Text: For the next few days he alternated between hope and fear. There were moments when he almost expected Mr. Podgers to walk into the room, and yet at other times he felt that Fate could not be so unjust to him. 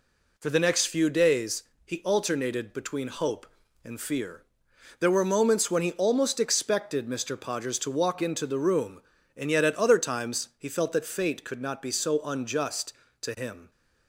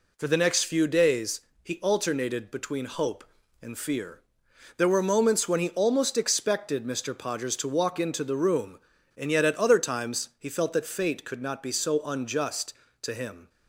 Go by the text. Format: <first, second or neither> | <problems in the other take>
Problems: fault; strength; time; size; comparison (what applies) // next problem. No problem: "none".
neither | pauses between "days" and "he"; slight; the same in both